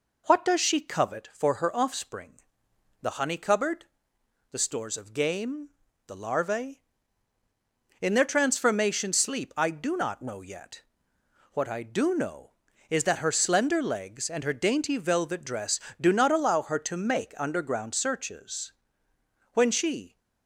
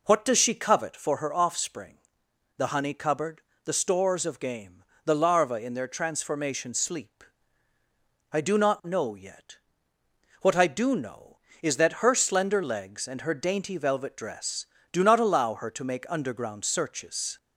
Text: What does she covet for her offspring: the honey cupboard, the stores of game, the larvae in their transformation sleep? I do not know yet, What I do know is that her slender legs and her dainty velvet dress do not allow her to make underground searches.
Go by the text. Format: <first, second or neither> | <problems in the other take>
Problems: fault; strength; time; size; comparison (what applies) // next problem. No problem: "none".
second | goes on to say "When she"; noticeable; from 19.5 s on; 0.64 s long